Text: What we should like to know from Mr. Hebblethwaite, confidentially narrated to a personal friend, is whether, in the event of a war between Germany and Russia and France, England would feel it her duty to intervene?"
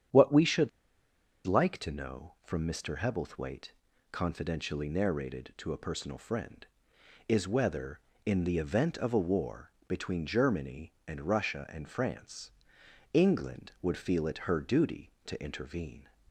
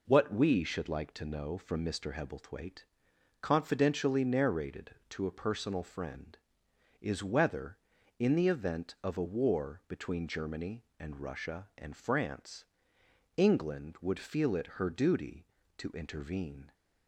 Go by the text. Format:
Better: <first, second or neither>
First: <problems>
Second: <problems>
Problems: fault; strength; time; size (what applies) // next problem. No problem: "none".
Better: second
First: starts louder than the rest; strong; until 1.9 s; 8.5 dB // pauses between "should" and "like"; noticeable; at 0.6 s; 0.77 s long // pauses between "war" and "between"; slight; at 9.7 s; 0.16 s long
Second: none